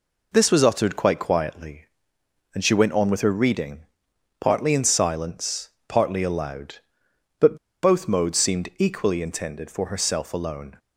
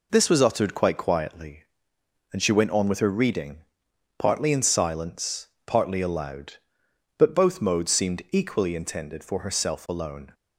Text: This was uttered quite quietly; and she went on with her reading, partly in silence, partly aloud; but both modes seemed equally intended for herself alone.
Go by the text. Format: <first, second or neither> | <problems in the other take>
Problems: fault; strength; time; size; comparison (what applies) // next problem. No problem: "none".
second | pauses between "but" and "both"; slight; at 7.5 s; 0.25 s long